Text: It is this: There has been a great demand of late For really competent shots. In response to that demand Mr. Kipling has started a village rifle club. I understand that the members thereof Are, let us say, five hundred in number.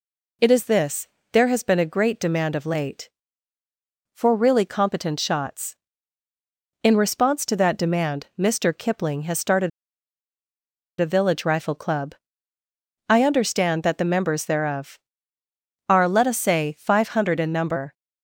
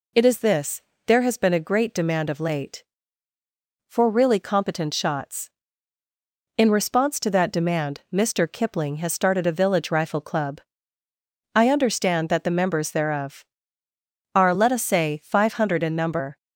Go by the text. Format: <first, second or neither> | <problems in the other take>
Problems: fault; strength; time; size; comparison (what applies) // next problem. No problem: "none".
second | pauses between "started" and "a"; strong; at 9.6 s; 1.3 s long